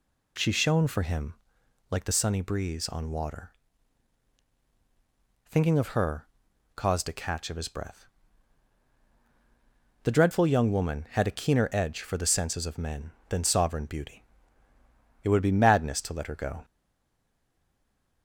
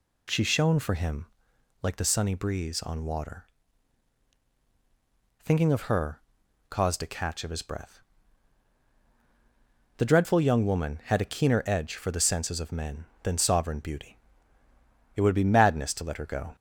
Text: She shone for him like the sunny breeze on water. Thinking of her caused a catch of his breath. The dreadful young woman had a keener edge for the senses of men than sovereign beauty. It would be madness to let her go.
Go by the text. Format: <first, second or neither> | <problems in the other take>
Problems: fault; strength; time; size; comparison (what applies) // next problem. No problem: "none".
second | pauses between "him" and "like"; noticeable; at 1.3 s; 0.56 s long; noticeable in the second // pauses between "her" and "caused"; noticeable; at 6.2 s; 0.48 s long; noticeable in the second // stays silent after the last word; noticeable; from 16.6 s on; 1.6 s long